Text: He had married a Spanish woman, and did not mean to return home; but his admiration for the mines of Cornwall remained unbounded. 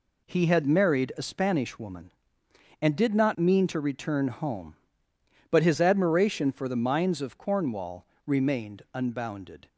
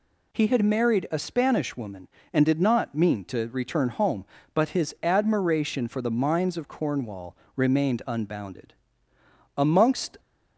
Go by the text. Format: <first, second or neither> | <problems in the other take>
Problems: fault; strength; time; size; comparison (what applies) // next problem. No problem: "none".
first | pauses between "Cornwall" and "remained"; slight; at 7.3 s; 0.20 s long; slight in the first // goes on to say "Amongst"; noticeable; from 9.5 s on; 0.62 s long